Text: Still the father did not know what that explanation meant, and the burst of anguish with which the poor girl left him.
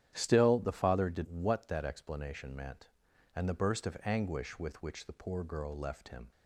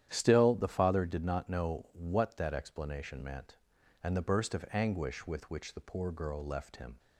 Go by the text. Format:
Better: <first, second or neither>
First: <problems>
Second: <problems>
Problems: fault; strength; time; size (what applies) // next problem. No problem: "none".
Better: second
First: starts louder than the rest; strong; until 1.1 s; 10.5 dB // skips "not know"; at 1.2 s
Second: starts louder than the rest; strong; until 1.1 s; 10.5 dB